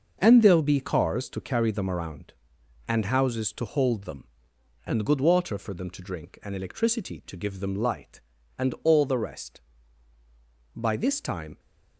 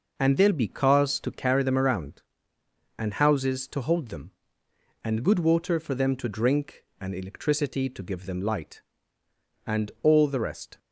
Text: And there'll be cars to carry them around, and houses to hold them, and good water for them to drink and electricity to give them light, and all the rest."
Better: second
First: goes on to say "By this time"; noticeable; from 10.7 s on; 0.84 s long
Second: none

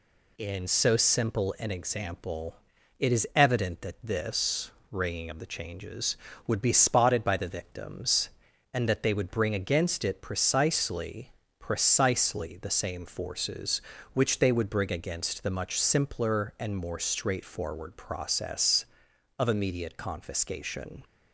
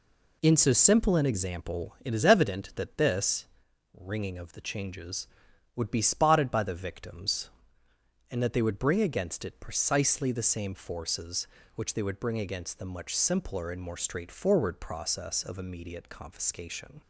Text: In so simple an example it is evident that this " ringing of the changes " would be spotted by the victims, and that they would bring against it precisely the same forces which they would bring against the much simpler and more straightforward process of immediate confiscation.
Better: second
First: pauses between "example" and "it"; at 2.5 s; 0.42 s long // says "precisely" twice; at 11.5 s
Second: none

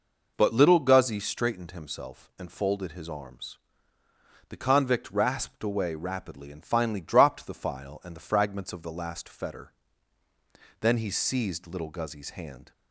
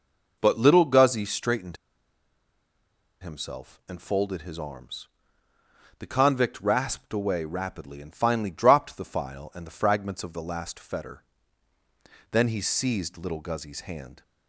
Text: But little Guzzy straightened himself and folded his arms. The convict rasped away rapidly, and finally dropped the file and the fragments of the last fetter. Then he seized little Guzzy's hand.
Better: first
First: none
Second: pauses between "straightened" and "himself"; strong; at 1.7 s; 1.4 s long

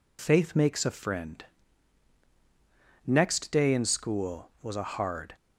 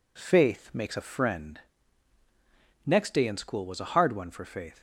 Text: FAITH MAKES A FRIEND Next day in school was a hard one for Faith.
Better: second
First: pauses between "FRIEND" and "Next"; strong; at 1.4 s; 1.6 s long // stops before "one for Faith"; at 5.3 s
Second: pauses between "FRIEND" and "Next"; strong; at 1.5 s; 1.2 s long

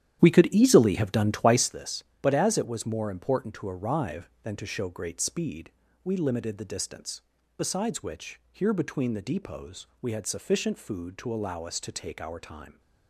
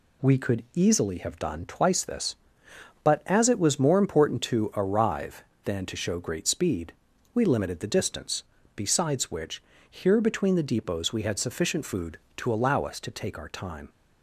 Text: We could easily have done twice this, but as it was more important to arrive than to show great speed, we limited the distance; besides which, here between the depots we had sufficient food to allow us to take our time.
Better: second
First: starts louder than the rest; strong; until 1.8 s; 11 dB // pauses between "depots" and "we"; slight; at 9.8 s; 0.16 s long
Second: none

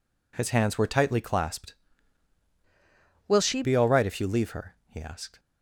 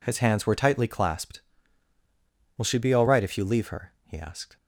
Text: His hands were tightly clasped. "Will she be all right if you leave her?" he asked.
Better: second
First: changes voice from "Will" to "she"; from 3.2 to 3.6 s; 0.4 s long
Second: none

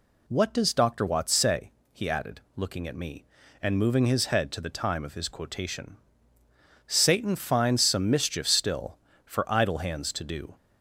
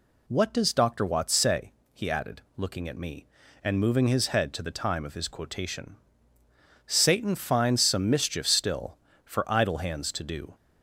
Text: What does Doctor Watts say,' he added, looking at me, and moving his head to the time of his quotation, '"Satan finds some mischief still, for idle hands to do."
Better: neither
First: none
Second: none

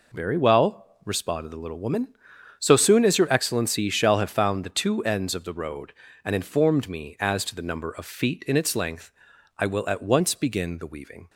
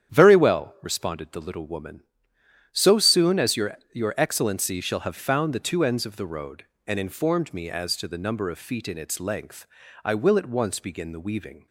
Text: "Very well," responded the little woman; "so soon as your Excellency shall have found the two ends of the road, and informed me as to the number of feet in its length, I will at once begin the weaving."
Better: first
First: none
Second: starts louder than the rest; strong; until 1.1 s; 9 dB // says "your" twice; at 3.9 s

